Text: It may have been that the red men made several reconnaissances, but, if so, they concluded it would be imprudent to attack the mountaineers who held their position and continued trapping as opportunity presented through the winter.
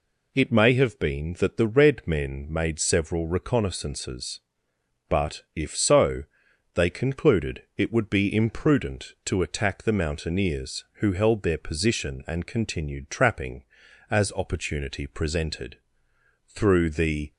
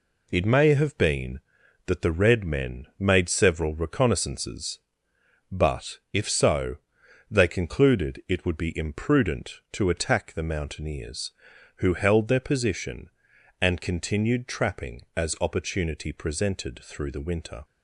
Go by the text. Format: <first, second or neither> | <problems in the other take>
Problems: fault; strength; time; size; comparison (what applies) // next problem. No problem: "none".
second | pauses between "presented" and "through"; noticeable; at 15.7 s; 0.68 s long // stops before "winter"; at 17.3 s